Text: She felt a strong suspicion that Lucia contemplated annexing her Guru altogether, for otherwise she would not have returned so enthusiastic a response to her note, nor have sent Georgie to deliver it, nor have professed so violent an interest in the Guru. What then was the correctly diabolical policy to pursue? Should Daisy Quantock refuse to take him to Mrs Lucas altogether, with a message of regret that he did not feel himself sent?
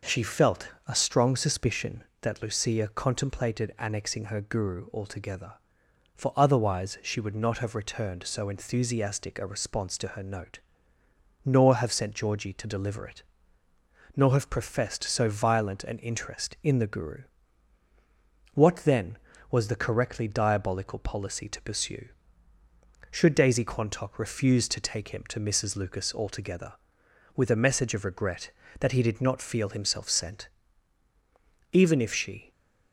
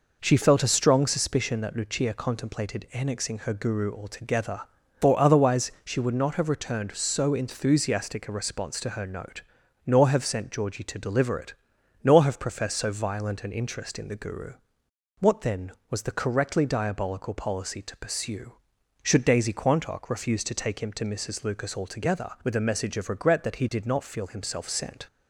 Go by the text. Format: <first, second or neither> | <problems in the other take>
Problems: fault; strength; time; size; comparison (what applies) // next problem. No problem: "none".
second | pauses between "felt" and "a"; slight; at 0.6 s; 0.19 s long // goes on to say "Even if she"; noticeable; from 31.7 s on; 0.78 s long